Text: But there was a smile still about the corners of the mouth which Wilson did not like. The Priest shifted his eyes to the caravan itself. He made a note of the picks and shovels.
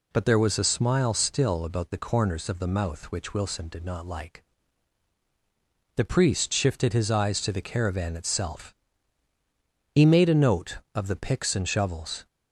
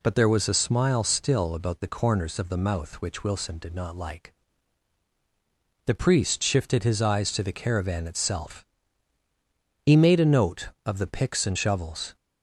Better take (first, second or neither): neither